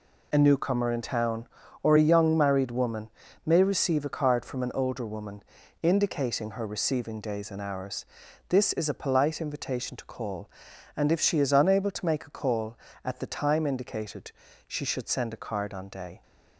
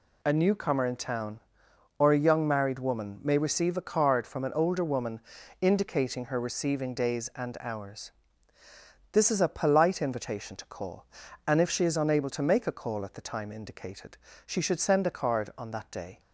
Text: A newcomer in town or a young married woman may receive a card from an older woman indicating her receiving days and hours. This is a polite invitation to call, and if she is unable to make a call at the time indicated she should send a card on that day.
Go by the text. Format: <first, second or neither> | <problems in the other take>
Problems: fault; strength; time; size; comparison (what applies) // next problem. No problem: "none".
second | pauses between "woman" and "may"; slight; at 3.0 s; 0.34 s long // pauses between "woman" and "indicating"; at 5.4 s; 0.38 s long; also in the second // pauses between "indicated" and "she"; slight; at 14.3 s; 0.34 s long; slight in the second // skips "that"; at 15.8 s